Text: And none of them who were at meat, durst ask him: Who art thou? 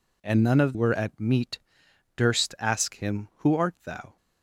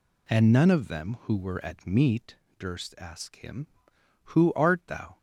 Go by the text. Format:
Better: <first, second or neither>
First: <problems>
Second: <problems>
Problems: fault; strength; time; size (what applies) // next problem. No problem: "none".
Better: second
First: skips "them who"; at 0.7 s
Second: none